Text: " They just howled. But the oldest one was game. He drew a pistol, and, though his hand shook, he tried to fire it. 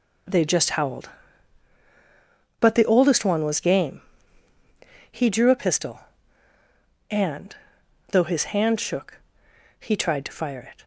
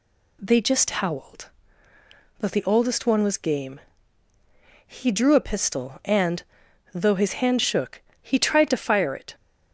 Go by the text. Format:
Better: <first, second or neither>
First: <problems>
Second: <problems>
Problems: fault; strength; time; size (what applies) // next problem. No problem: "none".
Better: neither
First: none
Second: none